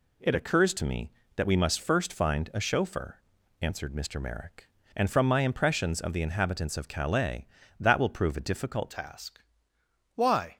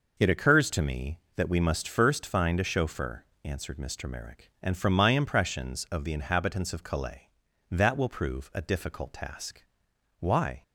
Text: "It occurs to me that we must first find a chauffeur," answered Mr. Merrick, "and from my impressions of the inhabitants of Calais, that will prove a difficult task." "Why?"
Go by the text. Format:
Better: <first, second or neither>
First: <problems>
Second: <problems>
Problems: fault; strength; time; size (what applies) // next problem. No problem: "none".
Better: second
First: changes voice at "task"; from 8.9 s on; 1.6 s long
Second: none